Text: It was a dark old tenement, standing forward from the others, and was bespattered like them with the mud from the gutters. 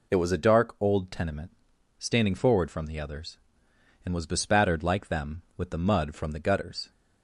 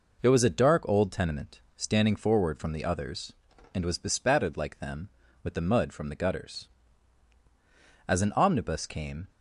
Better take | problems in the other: first | goes on to say "As an omnibus came"; noticeable; from 8.0 s on; 1.2 s long

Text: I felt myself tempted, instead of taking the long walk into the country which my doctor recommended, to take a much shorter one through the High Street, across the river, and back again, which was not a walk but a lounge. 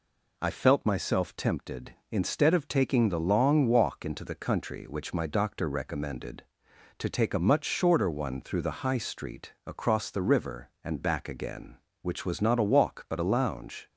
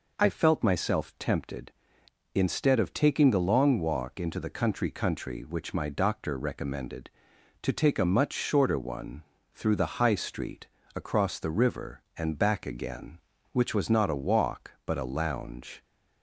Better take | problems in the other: first | says "country" twice; at 4.8 s // pauses between "one" and "through"; slight; at 9.2 s; 0.30 s long

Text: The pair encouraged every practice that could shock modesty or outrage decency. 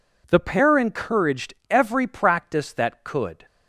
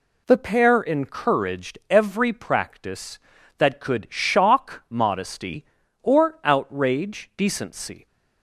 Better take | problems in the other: second | pauses between "encouraged" and "every"; slight; at 1.5 s; 0.16 s long // stops before "shock modesty or outrage decency"; at 3.4 s

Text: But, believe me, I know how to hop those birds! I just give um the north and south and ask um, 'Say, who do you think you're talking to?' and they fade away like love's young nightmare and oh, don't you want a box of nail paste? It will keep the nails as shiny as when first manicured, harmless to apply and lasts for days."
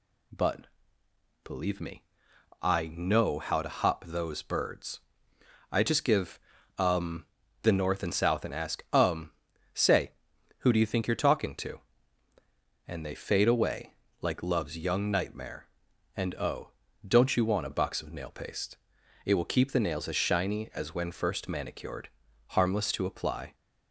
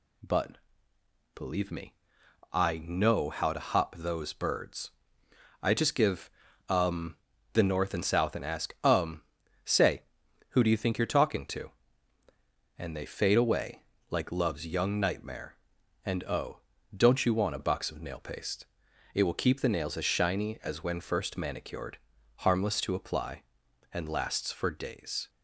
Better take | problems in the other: second | pauses between "give" and "um"; at 6.3 s; 0.40 s long; also in the second // pauses between "um" and "the"; at 7.2 s; 0.38 s long; also in the second // pauses between "away" and "like"; slight; at 13.9 s; 0.28 s long; slight in the second // stops before "and lasts for days"; at 23.5 s

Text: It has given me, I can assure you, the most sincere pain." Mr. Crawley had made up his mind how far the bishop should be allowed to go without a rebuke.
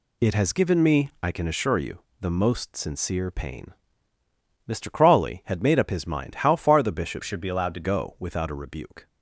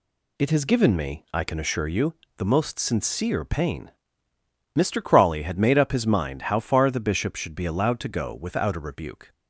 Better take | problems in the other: second | changes voice from "should" to "to"; from 7.2 to 7.8 s; 0.6 s long

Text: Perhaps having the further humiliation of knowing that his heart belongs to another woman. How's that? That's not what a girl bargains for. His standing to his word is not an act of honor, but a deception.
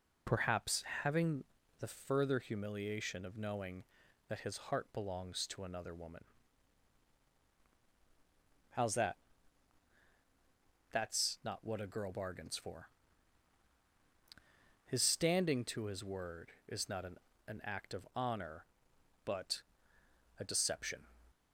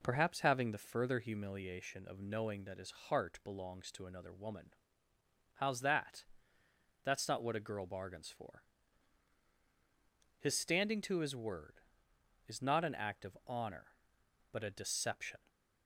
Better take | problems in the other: second | pauses between "Perhaps" and "having"; slight; at 0.8 s; 0.20 s long // pauses between "having" and "the"; slight; at 1.4 s; 0.36 s long // says "an" twice; at 17.4 s // pauses between "but" and "a"; noticeable; at 19.6 s; 0.76 s long

